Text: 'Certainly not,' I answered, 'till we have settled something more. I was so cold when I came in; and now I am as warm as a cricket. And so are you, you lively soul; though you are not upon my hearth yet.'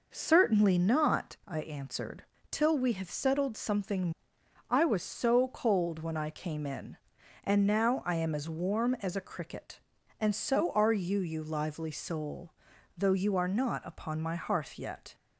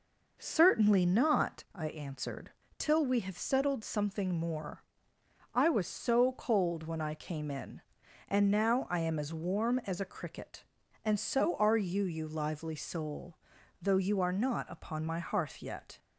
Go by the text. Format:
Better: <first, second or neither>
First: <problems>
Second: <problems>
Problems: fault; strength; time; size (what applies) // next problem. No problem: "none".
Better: second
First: skips "more"; at 4.4 s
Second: none